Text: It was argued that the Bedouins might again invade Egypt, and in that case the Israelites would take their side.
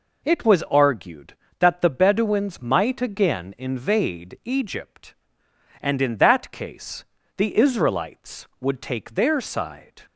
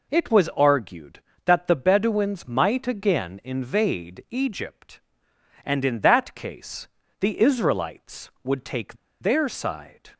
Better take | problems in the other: first | pauses between "case" and "the"; slight; at 6.8 s; 0.32 s long; slight in the first // pauses between "take" and "their"; slight; at 8.9 s; 0.25 s long

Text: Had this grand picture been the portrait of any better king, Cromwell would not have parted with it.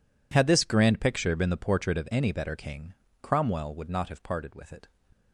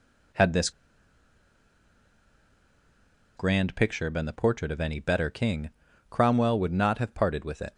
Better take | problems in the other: first | pauses between "this" and "grand"; strong; at 0.7 s; 2.6 s long

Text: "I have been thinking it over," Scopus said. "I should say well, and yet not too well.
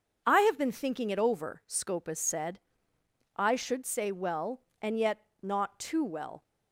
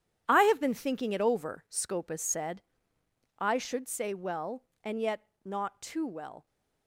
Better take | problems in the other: first | gets quieter; strong; throughout; 11 dB // starts louder than the rest; strong; until 1.2 s; 10 dB; also in the first // pauses between "yet" and "not"; slight; at 5.2 s; 0.16 s long; slight in the first

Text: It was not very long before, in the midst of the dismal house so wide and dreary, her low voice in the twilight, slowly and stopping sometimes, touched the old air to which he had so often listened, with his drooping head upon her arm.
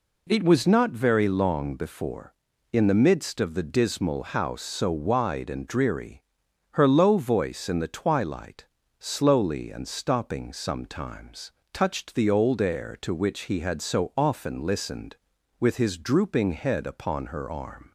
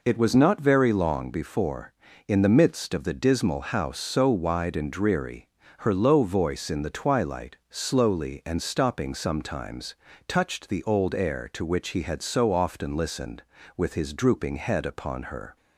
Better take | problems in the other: first | stops before "arm"; at 15.5 s

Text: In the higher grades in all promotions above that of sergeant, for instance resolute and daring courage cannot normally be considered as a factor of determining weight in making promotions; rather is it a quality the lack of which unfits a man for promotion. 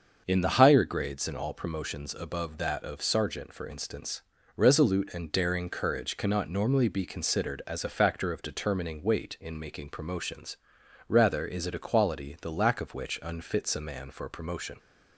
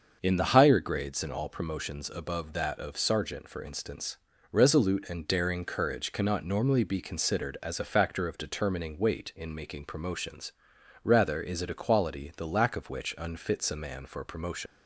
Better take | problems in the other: first | starts louder than the rest; until 1.2 s; 6.5 dB; also in the first // pauses between "instance" and "resolute"; slight; at 4.1 s; 0.34 s long; slight in the first // leaves "promotion" unfinished; at 14.6 s; 70 ms

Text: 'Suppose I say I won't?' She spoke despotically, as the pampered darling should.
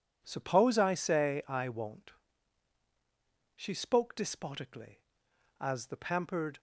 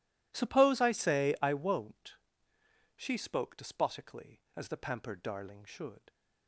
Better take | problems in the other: second | stops before "darling should"; at 6.5 s

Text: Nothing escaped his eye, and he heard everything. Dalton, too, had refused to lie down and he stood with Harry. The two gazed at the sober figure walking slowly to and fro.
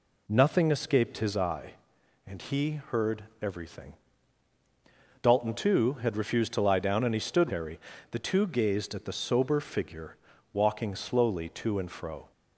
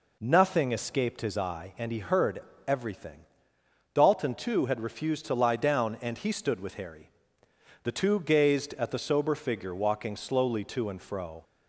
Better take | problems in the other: second | pauses between "heard" and "everything"; slight; at 3.2 s; 0.18 s long; slight in the second // skips "with"; at 7.4 s // pauses between "figure" and "walking"; slight; at 10.1 s; 0.36 s long

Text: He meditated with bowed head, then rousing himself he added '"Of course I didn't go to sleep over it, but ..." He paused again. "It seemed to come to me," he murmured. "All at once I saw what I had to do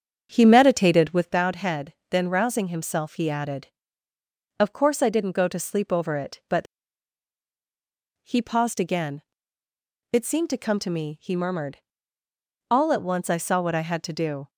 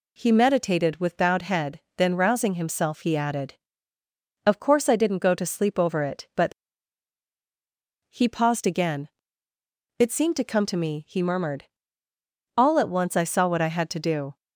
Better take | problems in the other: second | starts louder than the rest; strong; until 1.4 s; 8 dB

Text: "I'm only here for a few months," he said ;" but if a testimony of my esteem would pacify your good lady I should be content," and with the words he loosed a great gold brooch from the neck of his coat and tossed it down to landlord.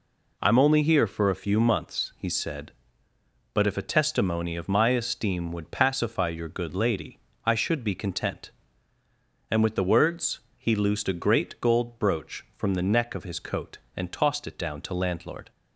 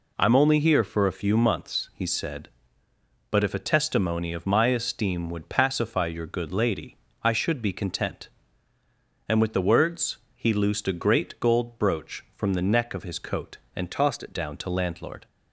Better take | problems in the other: first | pauses between "lady" and "I"; slight; at 6.9 s; 0.28 s long; slight in the first // pauses between "words" and "he"; slight; at 10.1 s; 0.18 s long; slight in the first // changes voice from "tossed" to "it"; from 13.9 to 14.3 s; 0.4 s long

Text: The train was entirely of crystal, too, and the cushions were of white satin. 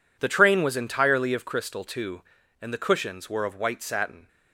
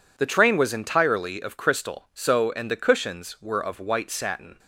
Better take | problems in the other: first | says "so" for "too"; at 2.1 s

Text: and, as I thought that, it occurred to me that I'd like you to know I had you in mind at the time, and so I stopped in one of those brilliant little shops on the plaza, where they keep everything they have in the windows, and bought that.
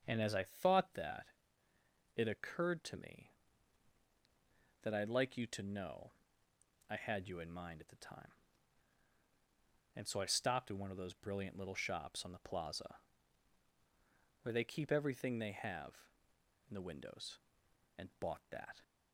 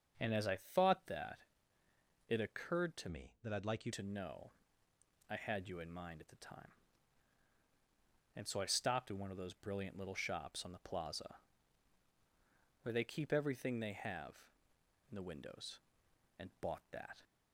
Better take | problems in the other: first | starts louder than the rest; until 1.2 s; 7 dB; strong in the first // changes voice from "me" to "you"; from 3.0 to 3.9 s; 0.9 s long // pauses between "know" and "I"; noticeable; at 4.5 s; 0.78 s long; noticeable in the first

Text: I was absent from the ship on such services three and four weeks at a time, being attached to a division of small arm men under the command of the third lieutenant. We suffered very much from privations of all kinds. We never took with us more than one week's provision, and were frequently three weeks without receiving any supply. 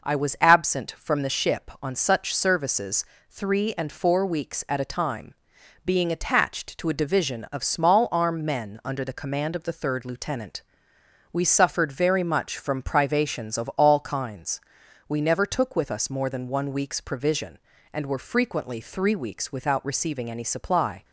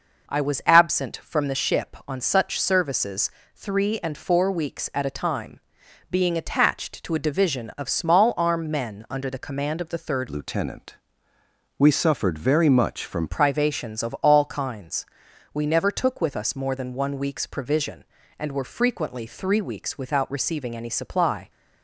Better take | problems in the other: first | pauses between "services" and "three"; slight; at 3.2 s; 0.24 s long; slight in the first // changes voice from "lieutenant" to "from"; from 10.2 to 13.2 s; 3.0 s long

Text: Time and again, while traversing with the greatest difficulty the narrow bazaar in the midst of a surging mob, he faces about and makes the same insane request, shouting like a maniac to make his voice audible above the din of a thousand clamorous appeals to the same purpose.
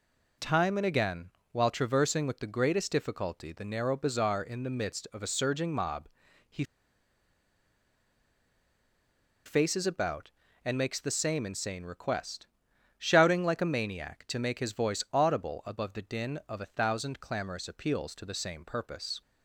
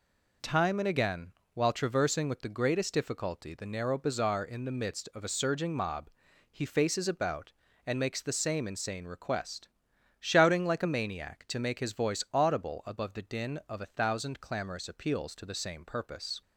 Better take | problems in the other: second | pauses between "he" and "faces"; strong; at 6.6 s; 2.8 s long

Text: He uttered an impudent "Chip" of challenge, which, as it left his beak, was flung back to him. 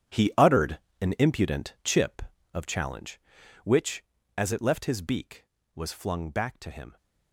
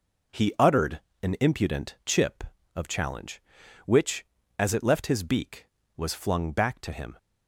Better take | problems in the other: second | gets quieter; strong; throughout; 14 dB // pauses between "uttered" and "an"; slight; at 0.7 s; 0.24 s long; slight in the second

